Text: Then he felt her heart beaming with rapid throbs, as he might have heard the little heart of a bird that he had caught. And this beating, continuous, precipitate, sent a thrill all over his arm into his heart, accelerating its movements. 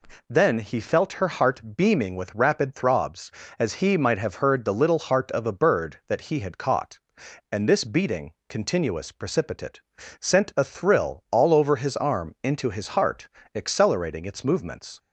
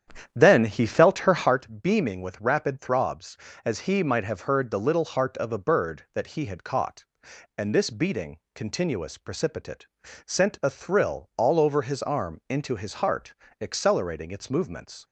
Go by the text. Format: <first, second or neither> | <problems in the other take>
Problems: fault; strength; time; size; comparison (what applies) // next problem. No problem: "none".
first | starts louder than the rest; strong; until 1.5 s; 9.5 dB